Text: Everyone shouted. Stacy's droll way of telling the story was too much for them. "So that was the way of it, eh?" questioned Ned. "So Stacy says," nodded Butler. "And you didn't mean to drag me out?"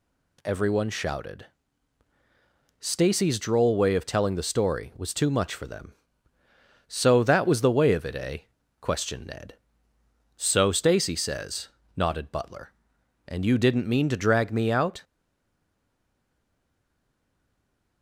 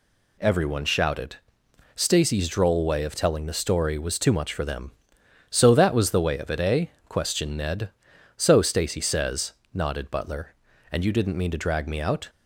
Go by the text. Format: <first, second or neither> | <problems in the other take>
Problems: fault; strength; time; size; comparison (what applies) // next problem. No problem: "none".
second | stays silent after the last word; strong; from 15.0 s on; 3.0 s long